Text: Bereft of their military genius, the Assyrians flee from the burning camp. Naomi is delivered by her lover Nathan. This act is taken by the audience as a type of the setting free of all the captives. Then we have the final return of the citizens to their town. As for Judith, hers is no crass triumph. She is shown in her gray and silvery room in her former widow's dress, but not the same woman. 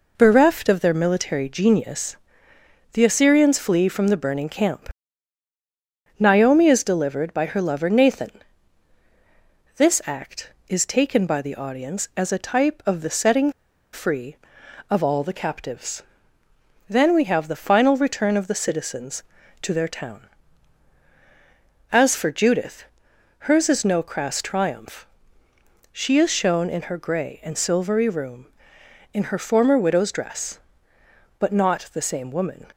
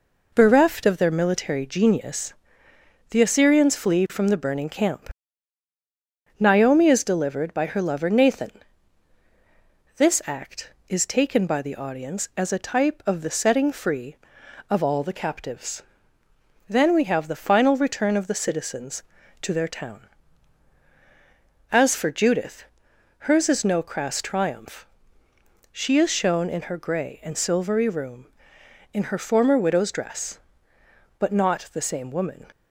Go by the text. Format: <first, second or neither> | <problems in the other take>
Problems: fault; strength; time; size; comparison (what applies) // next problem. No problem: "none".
second | pauses between "setting" and "free"; at 13.5 s; 0.41 s long